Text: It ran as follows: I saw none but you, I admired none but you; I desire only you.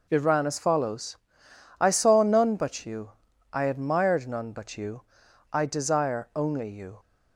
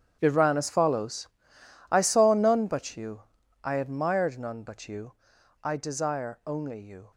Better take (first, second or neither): first